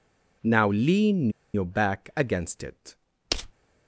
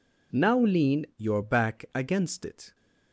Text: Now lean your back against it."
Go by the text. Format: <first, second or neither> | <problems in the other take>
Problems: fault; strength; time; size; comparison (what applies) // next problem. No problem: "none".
second | pauses between "lean" and "your"; slight; at 1.2 s; 0.24 s long